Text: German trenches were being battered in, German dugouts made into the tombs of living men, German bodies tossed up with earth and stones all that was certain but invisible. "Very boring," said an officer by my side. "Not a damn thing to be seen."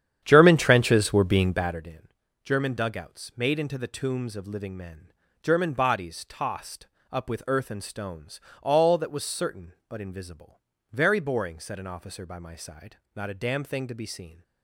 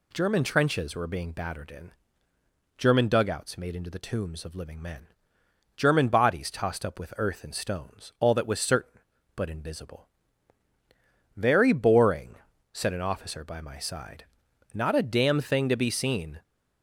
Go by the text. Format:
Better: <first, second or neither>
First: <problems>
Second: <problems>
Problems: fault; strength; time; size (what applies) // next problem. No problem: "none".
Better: second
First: starts louder than the rest; strong; until 1.8 s; 9.5 dB // pauses between "tossed" and "up"; slight; at 6.8 s; 0.24 s long // pauses between "stones" and "all"; slight; at 8.3 s; 0.24 s long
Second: none